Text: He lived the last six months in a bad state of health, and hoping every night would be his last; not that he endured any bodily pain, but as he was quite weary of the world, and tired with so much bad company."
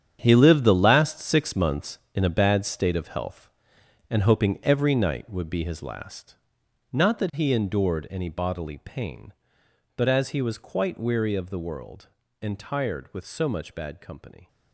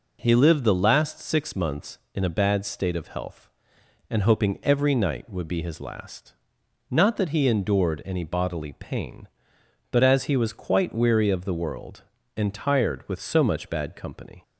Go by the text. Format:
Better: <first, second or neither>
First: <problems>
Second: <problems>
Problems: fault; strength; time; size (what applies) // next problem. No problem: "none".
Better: second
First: gets quieter; strong; throughout; 12.5 dB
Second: none